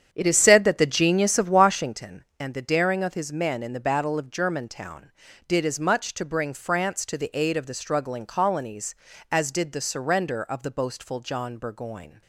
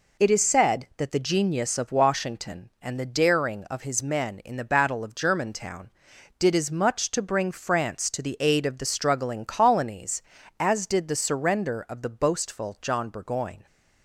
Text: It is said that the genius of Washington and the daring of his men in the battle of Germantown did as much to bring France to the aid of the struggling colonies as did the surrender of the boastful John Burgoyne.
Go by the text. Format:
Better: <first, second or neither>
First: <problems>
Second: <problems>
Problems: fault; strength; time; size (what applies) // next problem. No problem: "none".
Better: second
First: starts louder than the rest; strong; until 2.0 s; 8.5 dB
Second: none